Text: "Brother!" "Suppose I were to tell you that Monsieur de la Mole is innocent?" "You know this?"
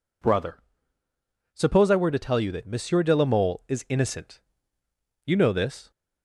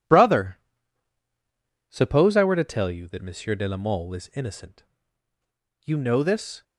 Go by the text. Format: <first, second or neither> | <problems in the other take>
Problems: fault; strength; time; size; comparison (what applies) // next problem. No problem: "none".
first | gets quieter; strong; throughout; 7.5 dB